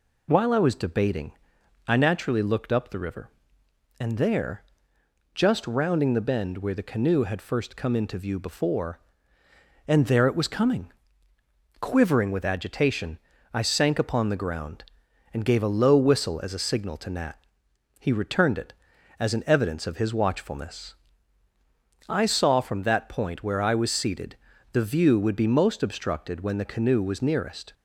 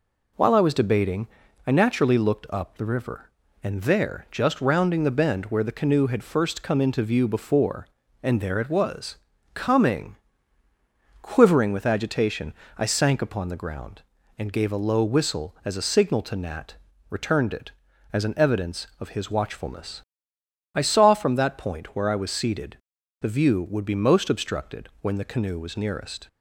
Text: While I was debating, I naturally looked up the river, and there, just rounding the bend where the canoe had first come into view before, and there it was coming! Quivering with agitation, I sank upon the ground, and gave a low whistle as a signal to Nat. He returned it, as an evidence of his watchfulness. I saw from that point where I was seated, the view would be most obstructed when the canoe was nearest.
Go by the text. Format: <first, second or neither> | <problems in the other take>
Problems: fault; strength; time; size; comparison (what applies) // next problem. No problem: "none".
first | pauses between "was" and "coming"; slight; at 9.1 s; 0.36 s long // skips "He"; at 16.9 s